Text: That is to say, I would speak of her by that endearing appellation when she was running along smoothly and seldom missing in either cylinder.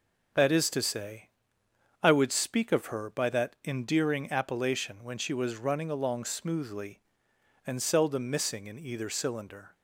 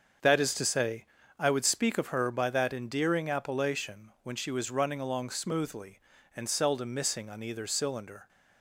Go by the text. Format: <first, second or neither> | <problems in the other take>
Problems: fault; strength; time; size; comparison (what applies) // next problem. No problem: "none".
first | starts louder than the rest; until 1.5 s; 7 dB; also in the first // says "on" for "in"; at 7.2 s